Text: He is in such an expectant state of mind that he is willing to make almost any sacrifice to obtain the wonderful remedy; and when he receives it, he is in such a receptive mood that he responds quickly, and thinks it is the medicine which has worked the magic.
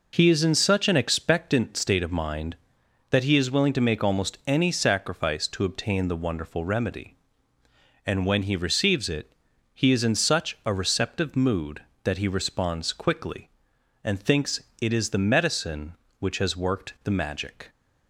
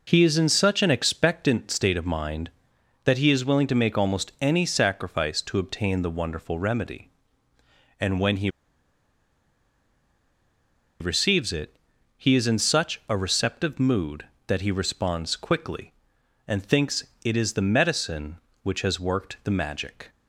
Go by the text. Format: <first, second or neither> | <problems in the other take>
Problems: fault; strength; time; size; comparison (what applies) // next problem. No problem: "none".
first | pauses between "he" and "receives"; strong; at 8.4 s; 2.5 s long // pauses between "thinks" and "it"; slight; at 17.0 s; 0.20 s long; slight in the first